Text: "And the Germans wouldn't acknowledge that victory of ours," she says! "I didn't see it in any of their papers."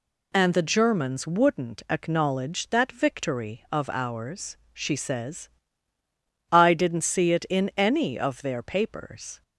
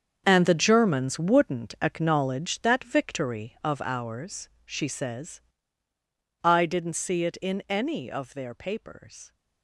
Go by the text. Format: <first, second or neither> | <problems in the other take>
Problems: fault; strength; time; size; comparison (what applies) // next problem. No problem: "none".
first | gets quieter; strong; throughout; 12 dB